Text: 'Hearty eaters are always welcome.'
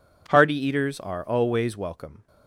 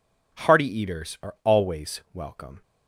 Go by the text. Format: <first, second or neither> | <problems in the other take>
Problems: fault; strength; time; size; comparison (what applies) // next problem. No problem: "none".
neither | none